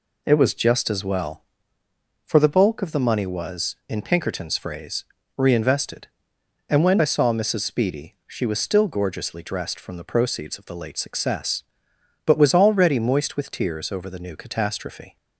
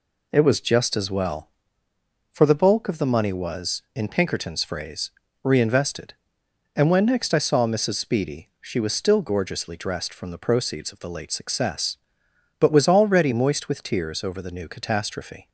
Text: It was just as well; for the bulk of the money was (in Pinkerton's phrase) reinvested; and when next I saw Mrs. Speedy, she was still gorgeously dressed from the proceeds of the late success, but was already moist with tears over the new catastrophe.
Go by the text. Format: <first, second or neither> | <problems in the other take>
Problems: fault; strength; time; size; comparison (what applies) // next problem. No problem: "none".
second | skips "next"; at 7.0 s